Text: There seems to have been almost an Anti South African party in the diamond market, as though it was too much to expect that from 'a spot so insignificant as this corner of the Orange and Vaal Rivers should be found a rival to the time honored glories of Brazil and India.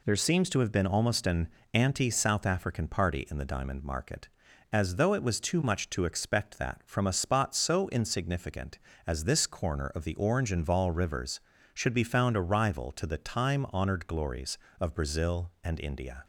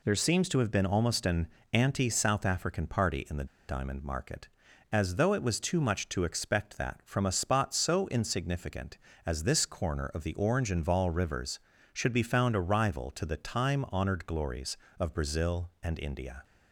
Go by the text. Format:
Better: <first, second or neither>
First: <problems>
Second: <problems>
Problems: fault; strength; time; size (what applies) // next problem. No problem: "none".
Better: first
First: pauses between "an" and "Anti"; slight; at 1.4 s; 0.24 s long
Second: pauses between "an" and "Anti"; slight; at 1.4 s; 0.24 s long // pauses between "the" and "diamond"; slight; at 3.4 s; 0.23 s long